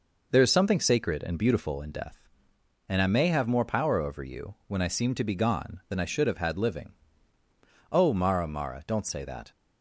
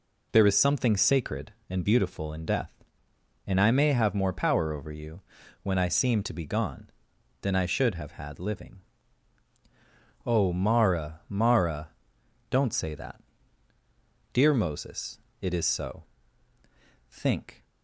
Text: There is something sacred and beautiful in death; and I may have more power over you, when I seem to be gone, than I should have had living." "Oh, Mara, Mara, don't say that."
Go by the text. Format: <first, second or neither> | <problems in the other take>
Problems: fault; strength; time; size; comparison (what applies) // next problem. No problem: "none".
first | goes on to say "Dear Moses it is so Think"; strong; from 14.3 s on; 3.3 s long